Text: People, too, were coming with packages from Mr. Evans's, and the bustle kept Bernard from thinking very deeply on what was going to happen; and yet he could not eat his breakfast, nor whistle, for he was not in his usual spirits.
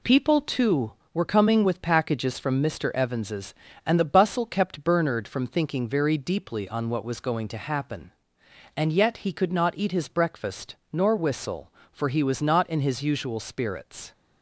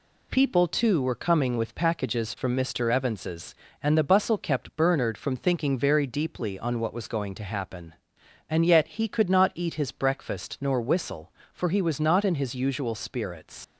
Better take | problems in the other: first | leaves "spirits" unfinished; at 13.6 s; 100 ms

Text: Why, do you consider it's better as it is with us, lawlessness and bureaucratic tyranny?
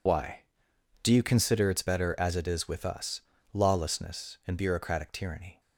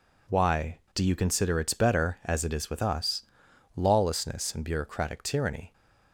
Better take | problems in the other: second | loses the start of "Why"; at 0.0 s; 40 ms

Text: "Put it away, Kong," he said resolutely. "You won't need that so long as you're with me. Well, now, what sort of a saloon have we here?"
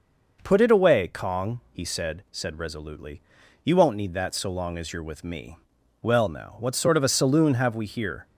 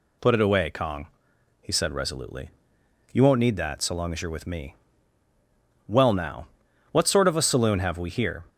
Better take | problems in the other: second | says "said" twice; at 2.3 s

